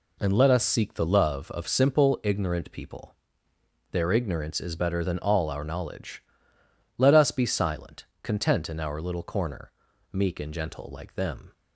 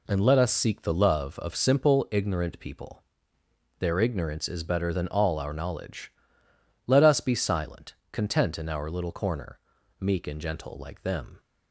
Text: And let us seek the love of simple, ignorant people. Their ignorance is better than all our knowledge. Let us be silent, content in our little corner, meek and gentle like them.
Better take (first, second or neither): neither